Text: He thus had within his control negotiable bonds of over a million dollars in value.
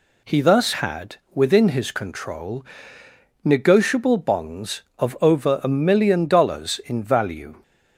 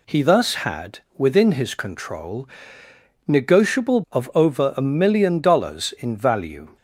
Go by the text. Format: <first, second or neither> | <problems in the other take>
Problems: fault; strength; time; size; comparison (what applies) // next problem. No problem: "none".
first | pauses between "had" and "within"; slight; at 0.9 s; 0.18 s long; slight in the first // pauses between "control" and "negotiable"; noticeable; at 2.4 s; 0.78 s long; noticeable in the first // skips "bonds"; at 4.0 s